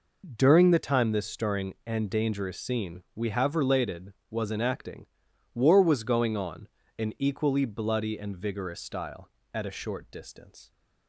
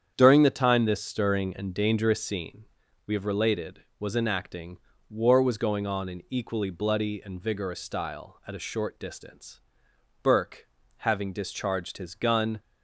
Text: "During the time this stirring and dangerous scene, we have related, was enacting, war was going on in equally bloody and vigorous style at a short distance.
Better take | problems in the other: first | starts louder than the rest; strong; until 1.1 s; 8.5 dB // goes on to say "Burke having discharged his gun"; strong; from 10.2 s on; 2.3 s long

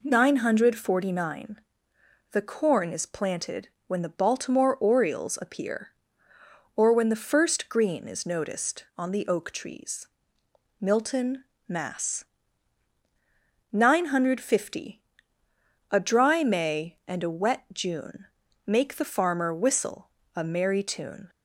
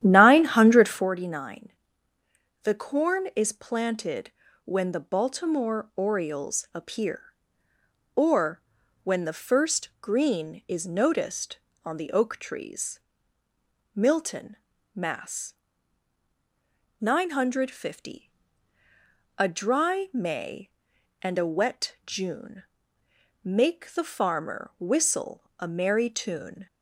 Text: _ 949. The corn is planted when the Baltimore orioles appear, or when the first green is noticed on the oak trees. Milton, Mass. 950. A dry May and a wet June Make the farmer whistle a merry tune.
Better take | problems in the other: first | starts louder than the rest; strong; until 1.1 s; 11.5 dB // pauses between "planted" and "when"; slight; at 4.3 s; 0.32 s long; slight in the first // pauses between "or" and "when"; at 8.6 s; 0.44 s long // pauses between "June" and "Make"; noticeable; at 22.6 s; 0.80 s long; also in the first // pauses between "whistle" and "a"; slight; at 25.4 s; 0.16 s long; slight in the first

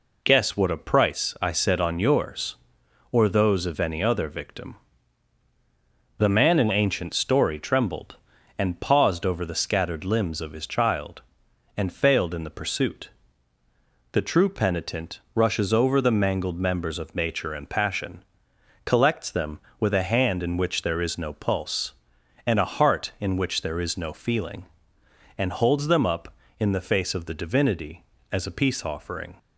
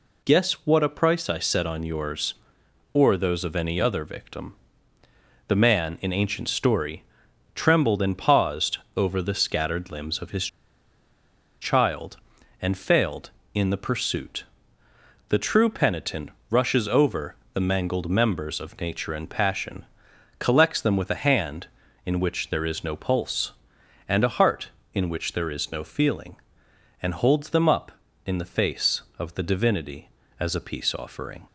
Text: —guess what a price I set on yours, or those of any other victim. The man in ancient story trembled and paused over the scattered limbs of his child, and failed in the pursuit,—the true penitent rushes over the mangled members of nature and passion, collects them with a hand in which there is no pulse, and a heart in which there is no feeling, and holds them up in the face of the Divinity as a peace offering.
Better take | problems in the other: first | pauses between "story" and "trembled"; noticeable; at 7.0 s; 0.52 s long // pauses between "paused" and "over"; slight; at 8.7 s; 0.16 s long // pauses between "his" and "child"; at 10.4 s; 1.1 s long // pauses between "penitent" and "rushes"; slight; at 16.2 s; 0.20 s long // pauses between "over" and "the"; slight; at 17.3 s; 0.20 s long

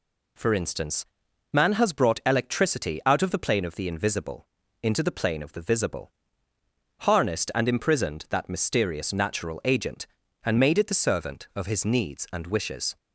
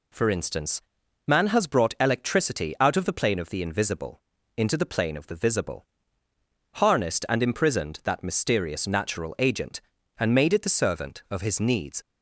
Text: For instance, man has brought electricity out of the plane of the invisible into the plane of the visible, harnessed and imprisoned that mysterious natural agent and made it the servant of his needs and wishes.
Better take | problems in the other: first | pauses between "invisible" and "into"; at 4.1 s; 0.38 s long; also in the first // stops before "and wishes"; at 12.0 s

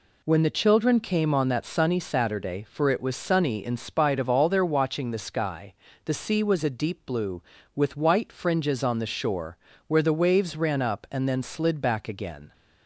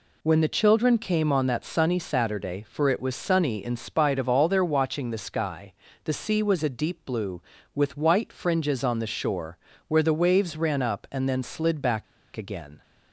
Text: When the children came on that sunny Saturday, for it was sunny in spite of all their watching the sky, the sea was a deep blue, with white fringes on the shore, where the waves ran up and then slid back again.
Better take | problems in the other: first | pauses between "back" and "again"; slight; at 12.0 s; 0.31 s long

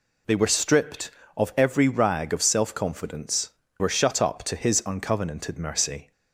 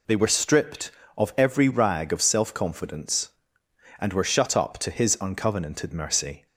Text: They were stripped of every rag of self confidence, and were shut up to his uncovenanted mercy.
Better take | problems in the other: second | skips "and"; at 3.6 s

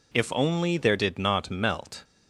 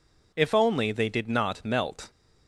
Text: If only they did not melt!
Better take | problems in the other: second | says "there" for "they"; at 0.7 s

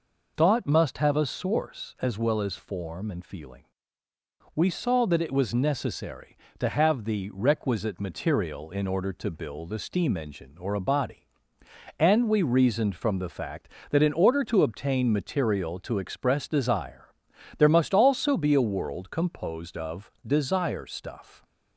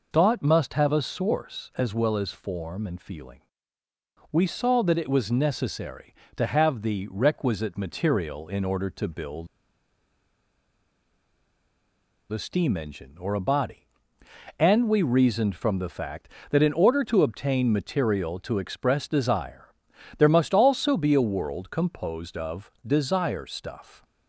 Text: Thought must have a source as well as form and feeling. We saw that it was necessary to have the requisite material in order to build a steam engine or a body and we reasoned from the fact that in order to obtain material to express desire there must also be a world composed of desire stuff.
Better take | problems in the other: first | pauses between "build" and "a"; strong; at 9.4 s; 2.8 s long // pauses between "desire" and "there"; noticeable; at 19.7 s; 0.46 s long; noticeable in the first // pauses between "of" and "desire"; slight; at 22.6 s; 0.16 s long; slight in the first

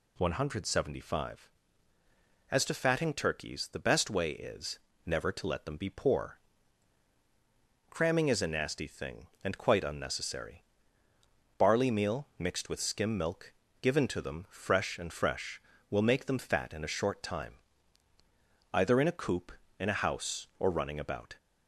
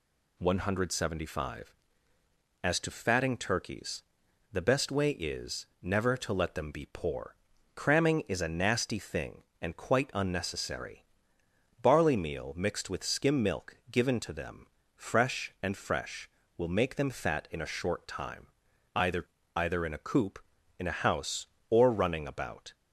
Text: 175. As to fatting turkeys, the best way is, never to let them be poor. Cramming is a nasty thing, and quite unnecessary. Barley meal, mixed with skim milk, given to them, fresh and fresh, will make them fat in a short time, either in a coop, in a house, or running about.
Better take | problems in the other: first | says "either" twice; at 19.5 s

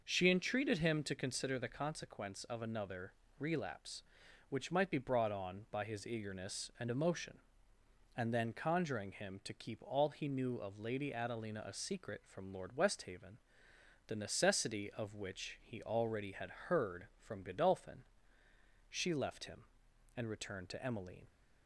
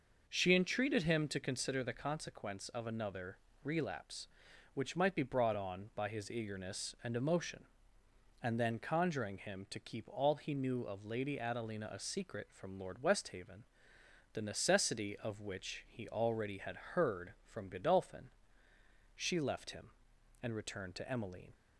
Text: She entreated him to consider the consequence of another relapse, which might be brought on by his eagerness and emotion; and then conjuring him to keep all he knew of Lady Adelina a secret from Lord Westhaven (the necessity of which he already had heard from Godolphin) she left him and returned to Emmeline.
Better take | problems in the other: neither | pauses between "another" and "relapse"; slight; the same in both

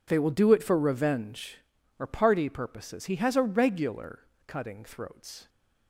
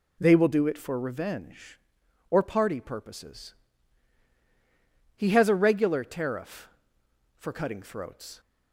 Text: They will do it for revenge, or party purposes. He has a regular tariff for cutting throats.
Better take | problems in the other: second | skips "tariff for"; at 4.3 s

